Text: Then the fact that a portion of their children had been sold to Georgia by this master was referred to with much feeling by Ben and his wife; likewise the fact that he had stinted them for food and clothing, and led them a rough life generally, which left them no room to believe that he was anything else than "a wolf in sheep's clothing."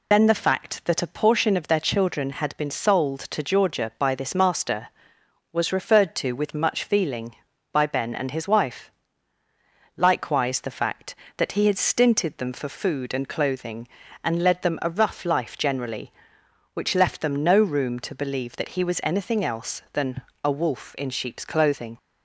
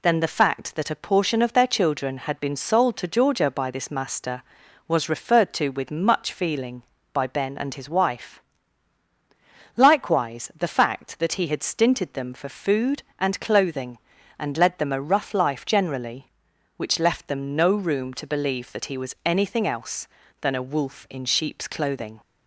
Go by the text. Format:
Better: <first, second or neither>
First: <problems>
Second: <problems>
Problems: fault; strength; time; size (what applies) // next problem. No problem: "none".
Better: second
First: loses the start of "Then"; at 0.1 s; 40 ms // pauses between "than" and "a"; slight; at 20.2 s; 0.22 s long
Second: none